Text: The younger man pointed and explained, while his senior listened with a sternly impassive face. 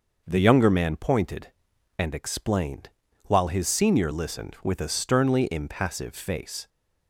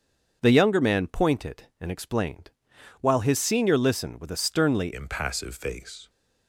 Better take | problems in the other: first | starts louder than the rest; until 1.4 s; 7 dB; noticeable in the first // changes voice at "impassive"; from 4.9 s on; 1.1 s long

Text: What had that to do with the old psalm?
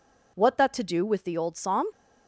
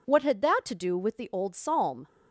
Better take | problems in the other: second | skips "had"; at 0.5 s

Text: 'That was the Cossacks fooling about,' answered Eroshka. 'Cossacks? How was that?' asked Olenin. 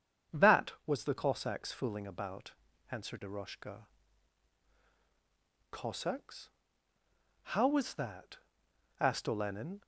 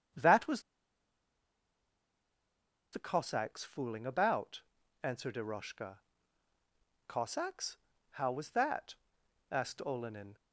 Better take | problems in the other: first | starts louder than the rest; strong; until 3.4 s; 7.5 dB; strong in the first // pauses between "was" and "the"; strong; at 0.6 s; 2.3 s long

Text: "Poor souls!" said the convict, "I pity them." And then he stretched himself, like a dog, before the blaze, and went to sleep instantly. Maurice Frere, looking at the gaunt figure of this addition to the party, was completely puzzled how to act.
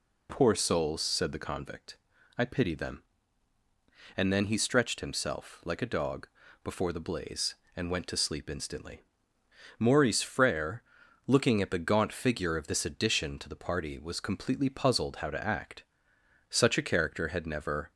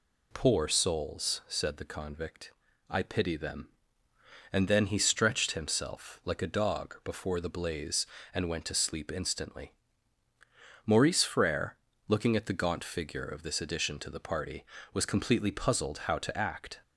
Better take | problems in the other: second | goes on to say "Such a character had never"; from 16.4 s on; 1.4 s long

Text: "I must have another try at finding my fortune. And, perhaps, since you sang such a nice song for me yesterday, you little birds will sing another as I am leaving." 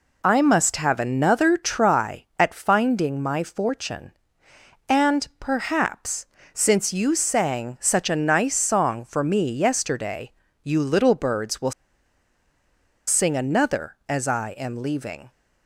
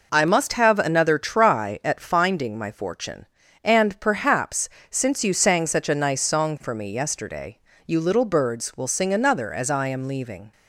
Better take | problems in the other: second | pauses between "will" and "sing"; strong; at 11.7 s; 1.3 s long

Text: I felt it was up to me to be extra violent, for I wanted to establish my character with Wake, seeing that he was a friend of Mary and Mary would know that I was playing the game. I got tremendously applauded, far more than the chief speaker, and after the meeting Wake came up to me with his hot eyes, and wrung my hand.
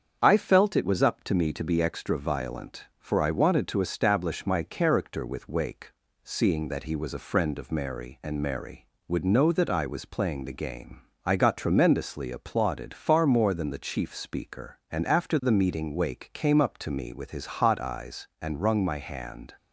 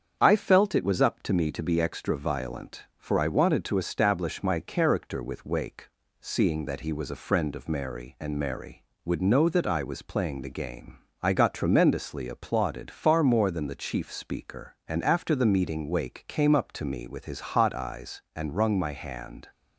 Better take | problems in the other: neither | starts louder than the rest; strong; the same in both

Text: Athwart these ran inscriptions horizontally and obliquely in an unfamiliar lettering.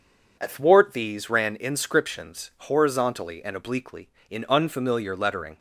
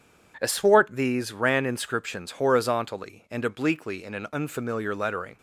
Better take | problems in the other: second | skips "an"; at 4.4 s

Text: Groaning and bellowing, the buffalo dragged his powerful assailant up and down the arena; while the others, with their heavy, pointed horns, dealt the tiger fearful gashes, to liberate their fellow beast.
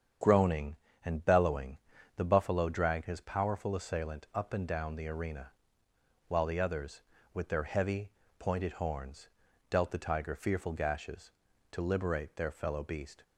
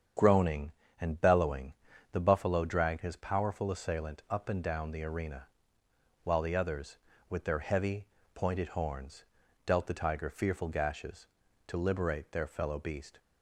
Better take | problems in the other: neither | starts louder than the rest; strong; the same in both

